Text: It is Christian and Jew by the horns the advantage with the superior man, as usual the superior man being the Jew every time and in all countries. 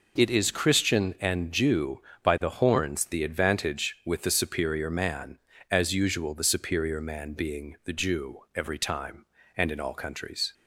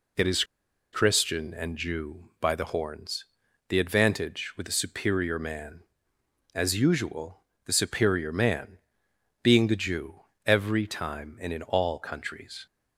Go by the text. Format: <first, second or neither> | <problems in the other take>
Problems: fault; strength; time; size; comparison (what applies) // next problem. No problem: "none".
first | pauses between "is" and "Christian"; noticeable; at 0.4 s; 0.49 s long // pauses between "horns" and "the"; noticeable; at 3.2 s; 0.46 s long // pauses between "usual" and "the"; slight; at 7.4 s; 0.24 s long // pauses between "man" and "being"; noticeable; at 8.7 s; 0.64 s long // pauses between "Jew" and "every"; slight; at 10.2 s; 0.24 s long